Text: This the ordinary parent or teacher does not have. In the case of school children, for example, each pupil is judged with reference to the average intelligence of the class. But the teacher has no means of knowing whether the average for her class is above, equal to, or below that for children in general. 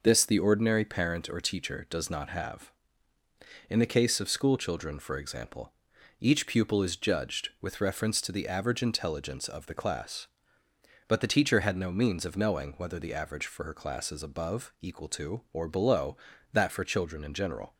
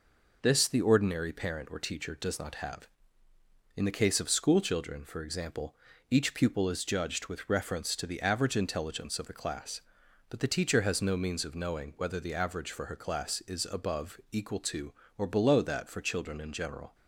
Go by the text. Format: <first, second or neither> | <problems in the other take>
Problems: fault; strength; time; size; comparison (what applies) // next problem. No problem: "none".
second | says "had" for "has"; at 11.6 s